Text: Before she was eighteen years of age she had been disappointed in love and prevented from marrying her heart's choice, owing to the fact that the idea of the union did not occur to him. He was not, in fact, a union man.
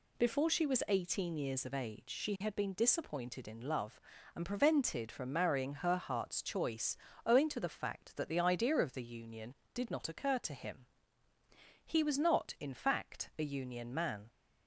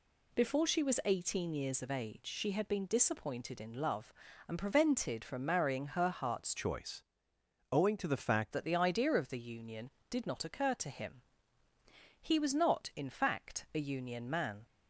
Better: first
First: none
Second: changes voice from "choice" to "fact"; from 6.5 to 8.5 s; 2.0 s long

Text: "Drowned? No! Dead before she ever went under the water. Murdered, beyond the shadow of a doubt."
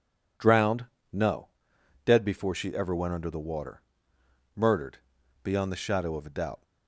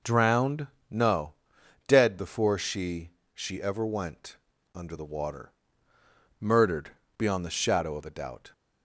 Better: first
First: none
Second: says "she" twice; at 3.3 s // pauses between "went" and "under"; slight; at 4.3 s; 0.36 s long

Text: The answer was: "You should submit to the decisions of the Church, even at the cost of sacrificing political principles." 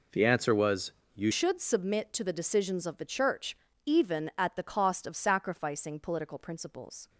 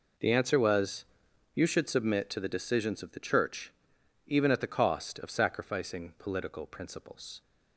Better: second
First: changes voice at "should"; from 1.3 s on; 5.7 s long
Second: none

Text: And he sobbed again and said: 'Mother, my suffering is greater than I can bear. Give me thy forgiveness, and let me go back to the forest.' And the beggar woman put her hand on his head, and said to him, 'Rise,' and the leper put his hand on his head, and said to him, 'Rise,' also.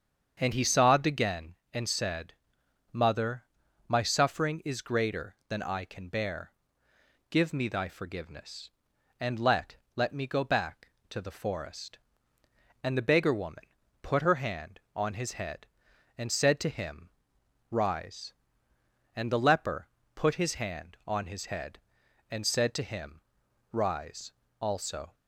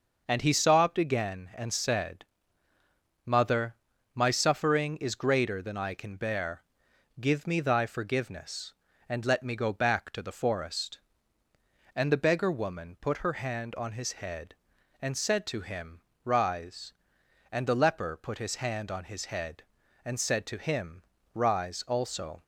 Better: second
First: starts louder than the rest; strong; until 1.4 s; 7.5 dB // says "let" twice; at 9.9 s // pauses between "woman" and "put"; at 13.6 s; 0.38 s long // pauses between "leper" and "put"; slight; at 19.8 s; 0.26 s long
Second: none

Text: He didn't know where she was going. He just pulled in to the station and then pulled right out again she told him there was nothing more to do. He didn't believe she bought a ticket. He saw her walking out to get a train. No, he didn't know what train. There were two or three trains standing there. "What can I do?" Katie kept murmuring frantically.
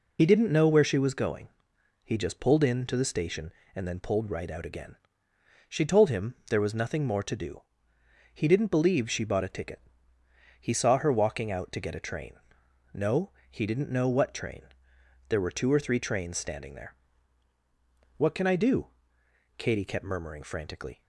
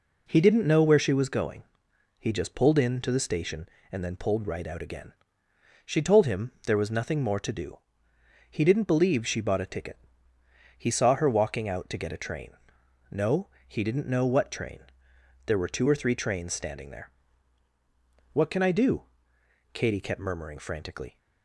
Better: second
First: loses the start of "He"; at 0.1 s; 70 ms // pauses between "again" and "she"; noticeable; at 4.9 s; 0.72 s long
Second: pauses between "again" and "she"; noticeable; at 5.1 s; 0.72 s long

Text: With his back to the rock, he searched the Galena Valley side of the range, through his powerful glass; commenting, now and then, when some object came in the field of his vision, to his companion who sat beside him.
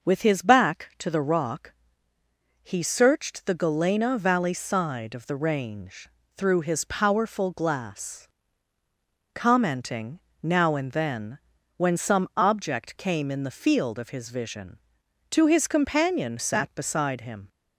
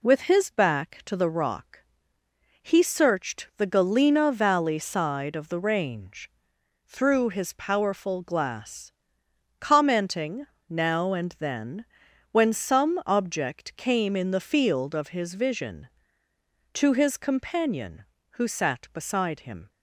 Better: second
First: starts louder than the rest; noticeable; until 1.1 s; 6 dB // skips "who"; at 16.3 s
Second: none

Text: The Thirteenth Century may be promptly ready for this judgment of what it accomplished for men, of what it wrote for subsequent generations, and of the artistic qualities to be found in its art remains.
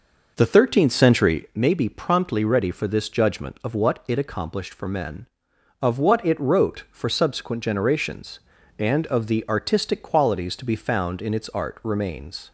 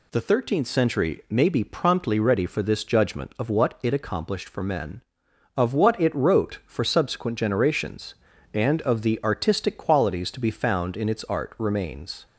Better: second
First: starts louder than the rest; noticeable; until 1.5 s; 5.5 dB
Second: none

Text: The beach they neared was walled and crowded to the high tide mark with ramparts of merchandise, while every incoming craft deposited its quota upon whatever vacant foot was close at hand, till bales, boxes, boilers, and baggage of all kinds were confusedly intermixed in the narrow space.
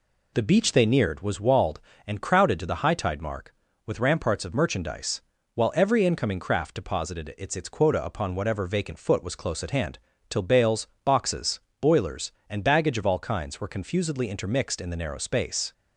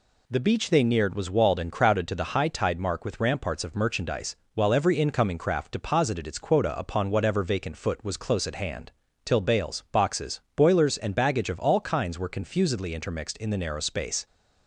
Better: second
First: says "its" twice; at 7.5 s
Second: none

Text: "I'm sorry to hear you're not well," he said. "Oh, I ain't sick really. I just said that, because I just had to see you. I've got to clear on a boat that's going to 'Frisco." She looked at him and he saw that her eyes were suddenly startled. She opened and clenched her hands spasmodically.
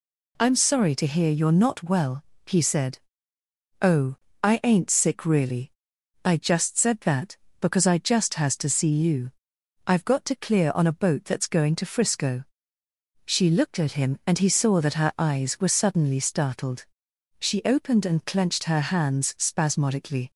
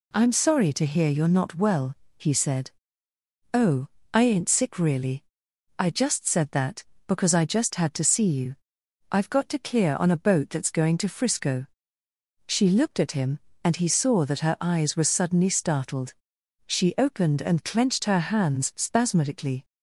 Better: second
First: says "has" for "had"; at 8.3 s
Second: none

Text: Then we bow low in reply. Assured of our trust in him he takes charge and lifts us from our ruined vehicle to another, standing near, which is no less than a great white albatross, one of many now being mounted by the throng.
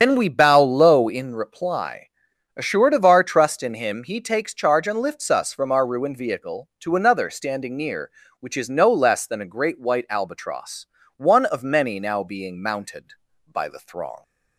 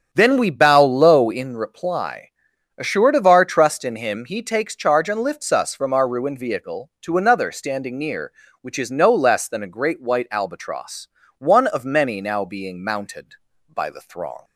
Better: second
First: loses the start of "Then"; at 0.0 s; 85 ms // starts louder than the rest; strong; until 1.0 s; 7.5 dB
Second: starts louder than the rest; strong; until 1.1 s; 8 dB

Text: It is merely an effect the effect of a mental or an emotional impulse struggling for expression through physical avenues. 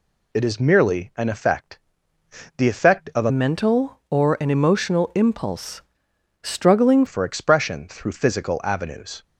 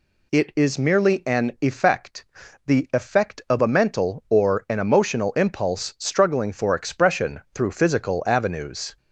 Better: second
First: pauses between "effect" and "the"; noticeable; at 1.7 s; 0.78 s long // changes voice from "mental" to "struggling"; from 3.3 to 7.0 s; 3.7 s long // pauses between "impulse" and "struggling"; noticeable; at 5.8 s; 0.62 s long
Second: pauses between "effect" and "the"; at 2.2 s; 0.44 s long

